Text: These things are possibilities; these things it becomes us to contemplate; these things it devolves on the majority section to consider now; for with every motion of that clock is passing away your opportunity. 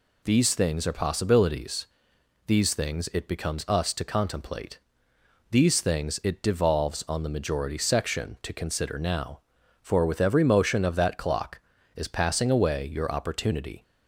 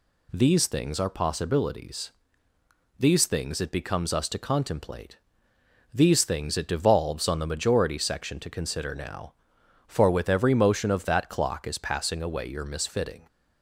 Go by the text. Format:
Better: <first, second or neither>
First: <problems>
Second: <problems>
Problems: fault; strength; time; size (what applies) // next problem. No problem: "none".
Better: first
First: none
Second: says "misfitting" for "opportunity"; at 12.6 s